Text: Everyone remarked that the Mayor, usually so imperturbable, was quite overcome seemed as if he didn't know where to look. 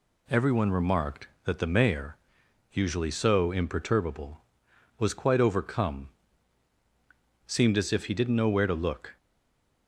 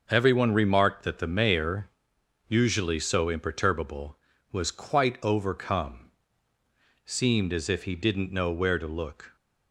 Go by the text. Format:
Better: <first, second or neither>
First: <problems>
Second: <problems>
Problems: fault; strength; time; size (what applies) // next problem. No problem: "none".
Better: second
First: pauses between "overcome" and "seemed"; strong; at 6.0 s; 1.3 s long // stays silent after the last word; slight; from 9.1 s on; 0.7 s long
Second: pauses between "overcome" and "seemed"; at 5.9 s; 1.0 s long